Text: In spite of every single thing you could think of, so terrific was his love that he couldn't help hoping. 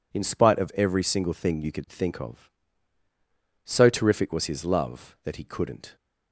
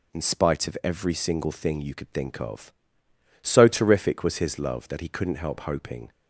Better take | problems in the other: second | stops before "help hoping"; at 5.9 s

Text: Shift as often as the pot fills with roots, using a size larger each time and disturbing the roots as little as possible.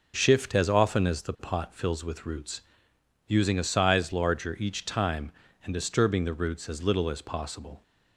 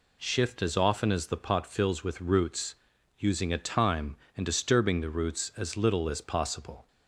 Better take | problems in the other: first | skips "size larger each"; at 3.5 s

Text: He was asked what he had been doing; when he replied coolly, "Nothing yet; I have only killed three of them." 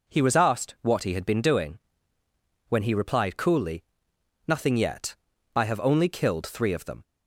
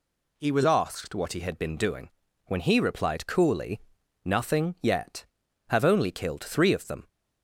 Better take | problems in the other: first | skips "I"; at 5.4 s

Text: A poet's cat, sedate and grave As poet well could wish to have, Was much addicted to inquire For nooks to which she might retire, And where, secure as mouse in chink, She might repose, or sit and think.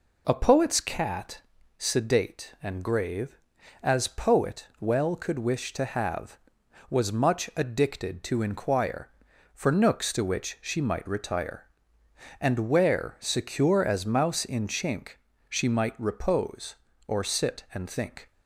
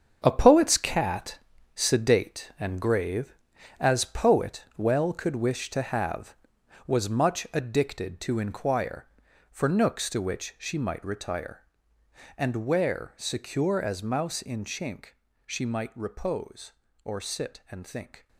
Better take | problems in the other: first | gets quieter; strong; throughout; 10 dB

